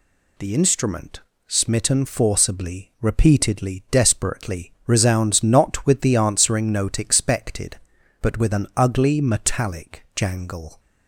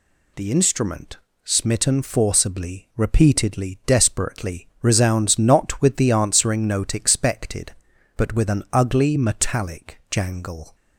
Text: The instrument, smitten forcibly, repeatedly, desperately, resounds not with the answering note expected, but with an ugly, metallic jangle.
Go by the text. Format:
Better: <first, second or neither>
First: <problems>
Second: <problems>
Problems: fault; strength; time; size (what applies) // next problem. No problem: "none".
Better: neither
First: none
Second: none